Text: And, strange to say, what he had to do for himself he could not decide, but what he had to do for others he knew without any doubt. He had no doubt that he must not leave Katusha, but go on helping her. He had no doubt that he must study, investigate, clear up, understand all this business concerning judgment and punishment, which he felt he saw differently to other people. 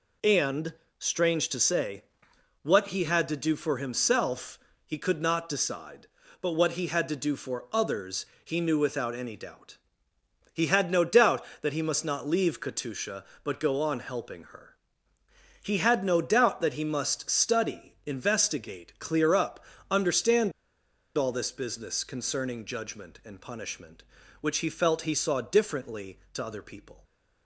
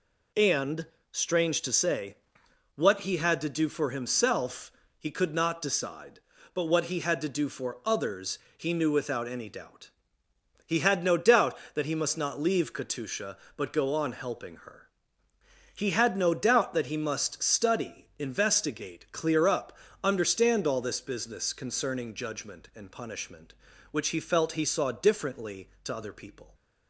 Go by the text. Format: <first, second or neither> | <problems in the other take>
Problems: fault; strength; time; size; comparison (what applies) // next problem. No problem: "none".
second | pauses between "himself" and "he"; slight; at 4.5 s; 0.28 s long; slight in the second // pauses between "others" and "he"; slight; at 8.2 s; 0.18 s long; slight in the second // pauses between "understand" and "all"; noticeable; at 20.5 s; 0.65 s long